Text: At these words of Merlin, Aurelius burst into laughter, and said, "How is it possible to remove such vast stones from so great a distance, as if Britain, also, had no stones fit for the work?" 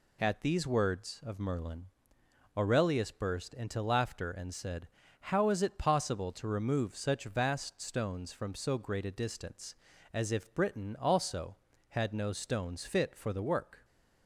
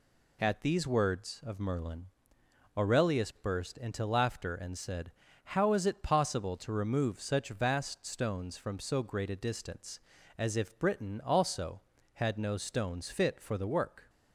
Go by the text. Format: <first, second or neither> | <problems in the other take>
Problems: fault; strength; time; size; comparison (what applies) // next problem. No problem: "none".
neither | none